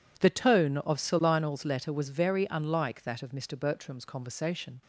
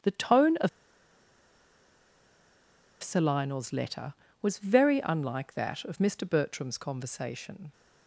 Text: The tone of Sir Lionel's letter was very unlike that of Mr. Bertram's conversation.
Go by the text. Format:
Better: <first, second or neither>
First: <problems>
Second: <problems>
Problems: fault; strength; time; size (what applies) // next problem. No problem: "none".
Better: first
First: none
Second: starts louder than the rest; strong; until 3.3 s; 9 dB // pauses between "of" and "Sir"; strong; at 0.6 s; 2.3 s long